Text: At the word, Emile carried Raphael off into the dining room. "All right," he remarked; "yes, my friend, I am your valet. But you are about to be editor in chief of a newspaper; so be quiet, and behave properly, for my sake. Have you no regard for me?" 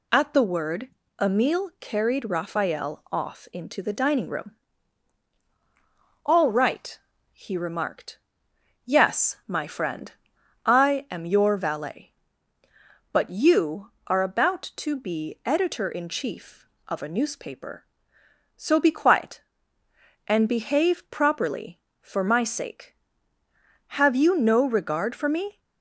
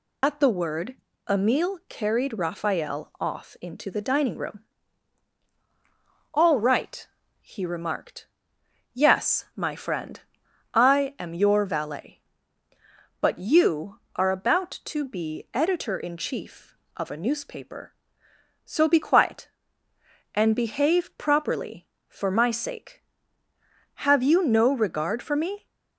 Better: first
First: none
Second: loses the start of "At"; at 0.2 s; 55 ms

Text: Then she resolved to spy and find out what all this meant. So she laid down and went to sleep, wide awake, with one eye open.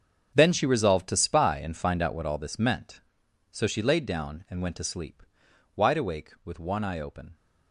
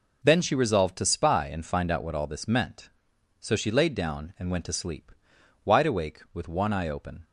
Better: second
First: gets quieter; strong; throughout; 14.5 dB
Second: none

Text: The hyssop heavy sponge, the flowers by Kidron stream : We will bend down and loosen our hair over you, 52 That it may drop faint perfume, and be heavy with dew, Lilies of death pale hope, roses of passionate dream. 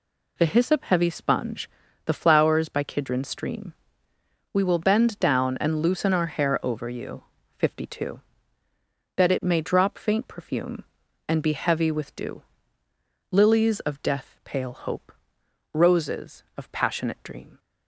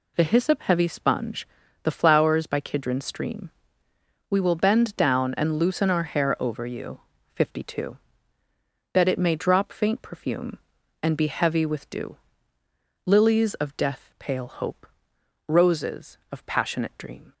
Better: neither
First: none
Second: none

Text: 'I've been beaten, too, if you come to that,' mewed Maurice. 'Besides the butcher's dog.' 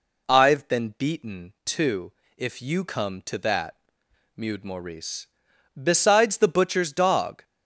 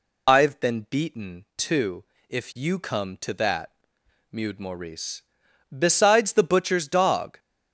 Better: first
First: none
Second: loses the start of "I've"; at 0.2 s; 95 ms

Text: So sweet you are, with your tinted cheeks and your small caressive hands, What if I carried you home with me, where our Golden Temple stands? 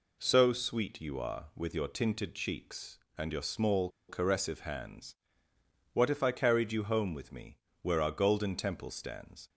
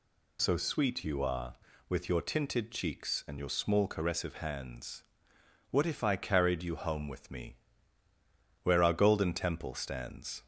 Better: second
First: pauses between "small" and "caressive"; slight; at 3.8 s; 0.20 s long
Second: none

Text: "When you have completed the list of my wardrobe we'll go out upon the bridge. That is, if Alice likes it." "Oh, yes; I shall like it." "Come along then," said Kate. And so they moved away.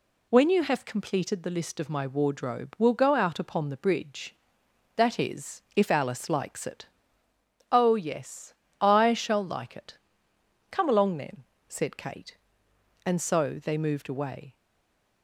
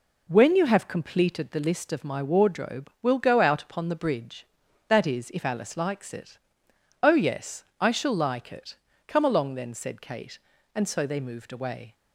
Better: second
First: stays silent after the last word; slight; from 14.5 s on; 0.7 s long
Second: none

